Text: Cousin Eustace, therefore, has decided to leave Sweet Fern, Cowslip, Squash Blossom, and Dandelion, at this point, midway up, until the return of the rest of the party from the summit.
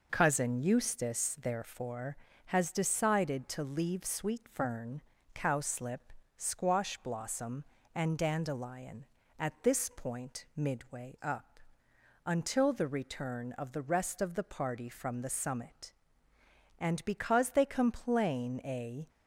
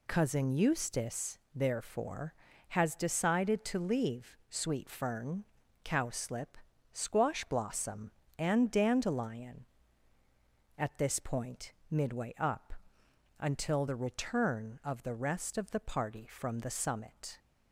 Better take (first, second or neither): second